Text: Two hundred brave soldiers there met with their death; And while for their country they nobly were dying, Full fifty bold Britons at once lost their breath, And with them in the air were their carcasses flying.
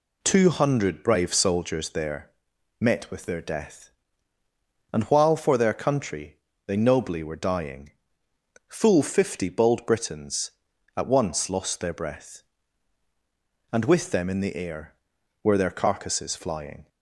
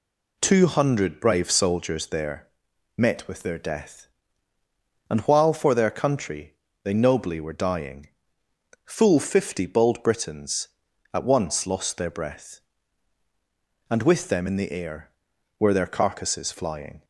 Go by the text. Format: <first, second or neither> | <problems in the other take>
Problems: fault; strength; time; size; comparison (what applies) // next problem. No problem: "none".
neither | pauses between "there" and "met"; noticeable; the same in both // pauses between "country" and "they"; slight; the same in both